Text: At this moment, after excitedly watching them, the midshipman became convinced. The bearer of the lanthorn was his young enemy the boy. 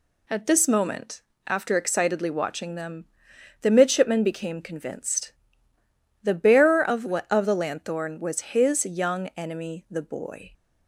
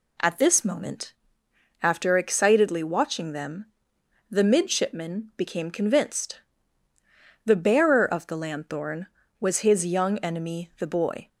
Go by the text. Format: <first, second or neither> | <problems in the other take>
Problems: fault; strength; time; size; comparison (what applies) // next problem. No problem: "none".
second | says "of" twice; at 7.3 s